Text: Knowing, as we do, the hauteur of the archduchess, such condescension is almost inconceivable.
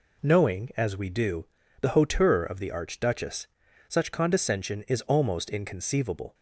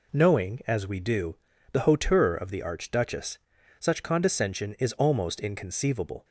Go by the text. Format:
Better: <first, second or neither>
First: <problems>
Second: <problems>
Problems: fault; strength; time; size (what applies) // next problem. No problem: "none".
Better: neither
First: none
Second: none